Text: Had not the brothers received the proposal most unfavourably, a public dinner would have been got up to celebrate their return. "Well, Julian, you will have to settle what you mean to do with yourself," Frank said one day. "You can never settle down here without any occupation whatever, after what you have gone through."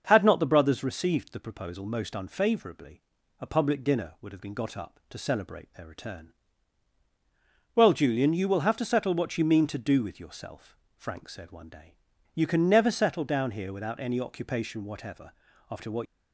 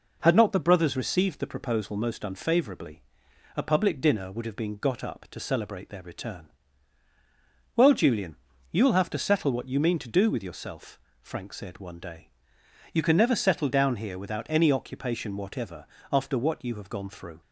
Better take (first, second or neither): second